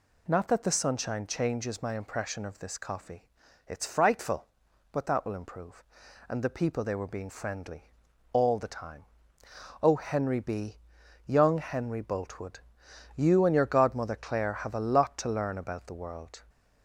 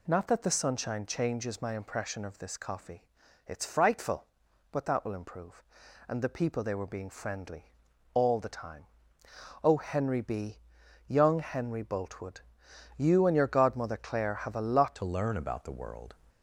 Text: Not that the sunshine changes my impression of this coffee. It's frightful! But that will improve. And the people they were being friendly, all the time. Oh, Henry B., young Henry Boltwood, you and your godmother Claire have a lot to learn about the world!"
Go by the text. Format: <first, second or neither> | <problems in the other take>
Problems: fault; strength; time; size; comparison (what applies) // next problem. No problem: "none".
first | changes voice at "to"; from 14.9 s on; 1.2 s long